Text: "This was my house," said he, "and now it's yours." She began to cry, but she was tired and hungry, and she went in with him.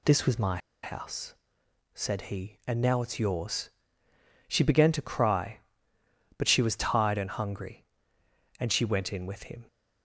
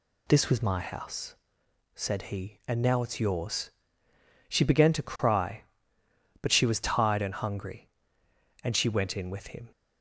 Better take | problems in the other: second | pauses between "my" and "house"; slight; at 0.5 s; 0.25 s long

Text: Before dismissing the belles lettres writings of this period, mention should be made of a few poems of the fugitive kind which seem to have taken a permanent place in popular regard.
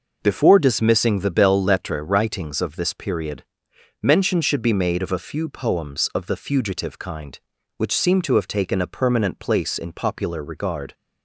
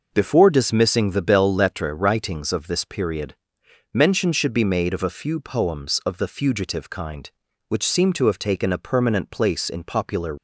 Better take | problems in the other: first | stops before "regard"; at 10.3 s

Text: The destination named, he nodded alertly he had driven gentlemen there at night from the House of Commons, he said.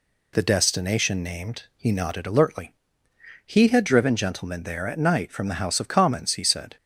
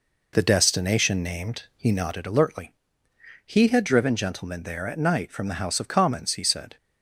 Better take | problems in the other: first | starts louder than the rest; noticeable; until 2.1 s; 4.5 dB // pauses between "alertly" and "he"; noticeable; at 2.7 s; 0.74 s long; noticeable in the first

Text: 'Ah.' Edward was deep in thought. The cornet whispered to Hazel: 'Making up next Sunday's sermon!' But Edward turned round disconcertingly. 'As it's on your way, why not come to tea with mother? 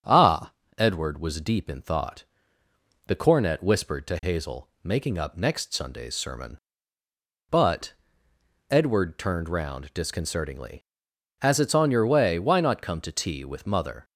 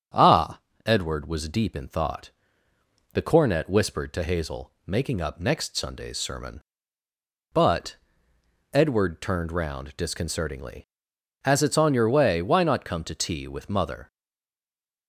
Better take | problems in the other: first | starts louder than the rest; strong; until 1.4 s; 7.5 dB; strong in the first // pauses between "But" and "Edward"; noticeable; at 7.9 s; 0.78 s long; noticeable in the first // stays silent after the last word; from 14.1 s on; 0.9 s long

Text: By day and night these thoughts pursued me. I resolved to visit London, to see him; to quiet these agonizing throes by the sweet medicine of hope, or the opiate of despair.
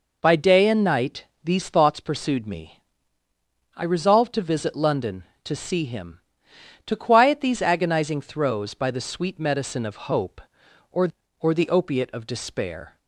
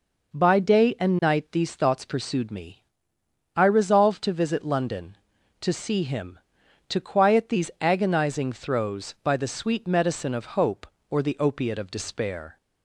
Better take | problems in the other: second | pauses between "night" and "these"; slight; at 1.2 s; 0.18 s long // says "or" twice; at 11.3 s

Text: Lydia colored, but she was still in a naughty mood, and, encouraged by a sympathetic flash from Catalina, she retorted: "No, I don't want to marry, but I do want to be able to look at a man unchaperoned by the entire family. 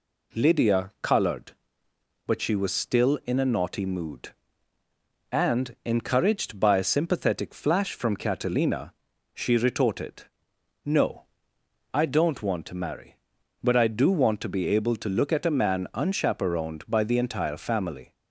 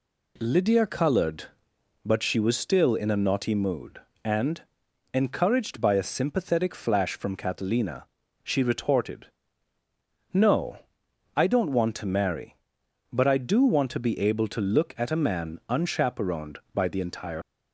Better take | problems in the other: first | stops before "family"; at 17.4 s

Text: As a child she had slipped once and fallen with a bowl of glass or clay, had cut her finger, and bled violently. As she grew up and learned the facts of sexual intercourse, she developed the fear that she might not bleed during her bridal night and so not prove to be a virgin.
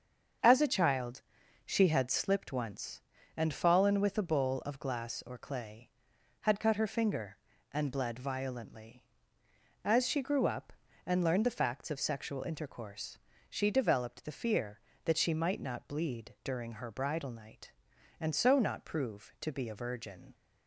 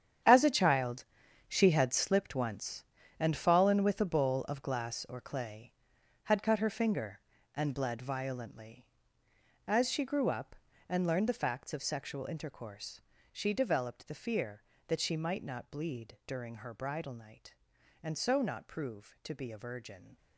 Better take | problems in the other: first | gets quieter; strong; throughout; 12.5 dB // starts louder than the rest; strong; until 1.6 s; 9 dB; also in the first // pauses between "child" and "she"; at 1.0 s; 0.42 s long; also in the first

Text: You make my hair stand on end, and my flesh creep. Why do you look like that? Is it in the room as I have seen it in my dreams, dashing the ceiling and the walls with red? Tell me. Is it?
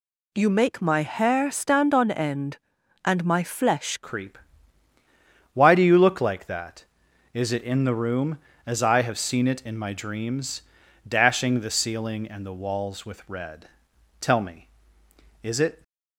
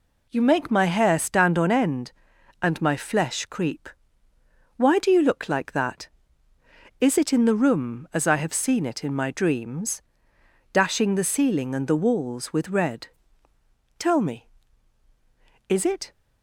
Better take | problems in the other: second | changes voice at "creep"; from 4.0 s on; 11.8 s long

